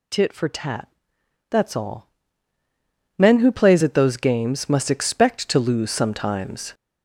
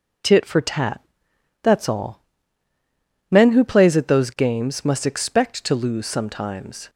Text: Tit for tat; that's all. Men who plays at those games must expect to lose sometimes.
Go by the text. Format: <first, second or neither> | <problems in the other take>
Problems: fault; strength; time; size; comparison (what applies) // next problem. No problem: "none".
second | gets louder; noticeable; throughout; 5 dB